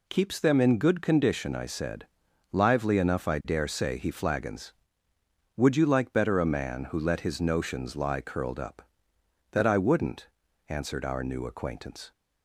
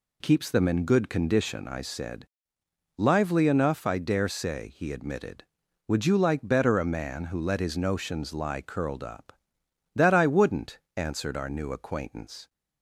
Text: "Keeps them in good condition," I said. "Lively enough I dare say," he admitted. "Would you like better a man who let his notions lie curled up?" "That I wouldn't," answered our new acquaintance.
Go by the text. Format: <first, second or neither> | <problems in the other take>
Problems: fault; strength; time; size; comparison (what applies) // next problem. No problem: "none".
second | says "flagons" for "admitted"; at 4.0 s